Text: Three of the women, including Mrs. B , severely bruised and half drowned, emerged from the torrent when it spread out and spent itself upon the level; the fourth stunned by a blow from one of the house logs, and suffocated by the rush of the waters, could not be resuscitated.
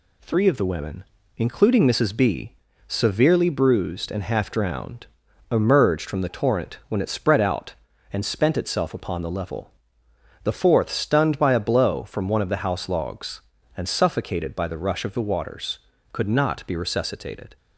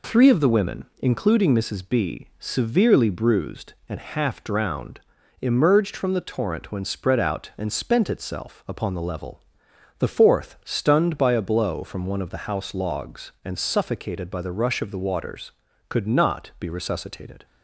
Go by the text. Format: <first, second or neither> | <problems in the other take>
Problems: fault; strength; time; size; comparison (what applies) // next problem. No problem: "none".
first | skips "it"; at 6.8 s